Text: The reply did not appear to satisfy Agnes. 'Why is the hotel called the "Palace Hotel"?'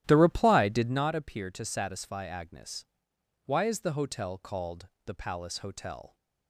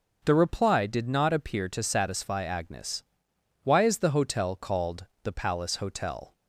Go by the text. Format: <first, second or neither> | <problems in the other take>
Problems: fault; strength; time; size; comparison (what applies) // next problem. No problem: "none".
second | starts louder than the rest; strong; until 1.1 s; 13 dB // pauses between "called" and "the"; slight; at 4.8 s; 0.18 s long; slight in the second